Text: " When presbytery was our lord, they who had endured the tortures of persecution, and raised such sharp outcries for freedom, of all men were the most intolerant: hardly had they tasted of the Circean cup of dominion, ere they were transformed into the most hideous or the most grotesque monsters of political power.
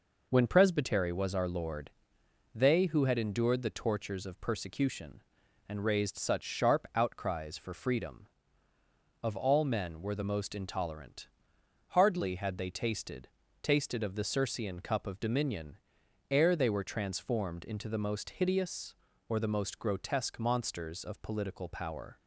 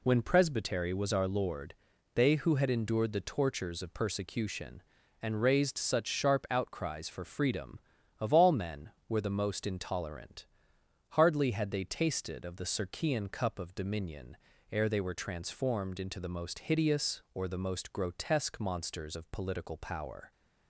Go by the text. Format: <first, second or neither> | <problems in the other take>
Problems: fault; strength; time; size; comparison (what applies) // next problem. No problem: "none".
second | says "tasted" twice; at 13.6 s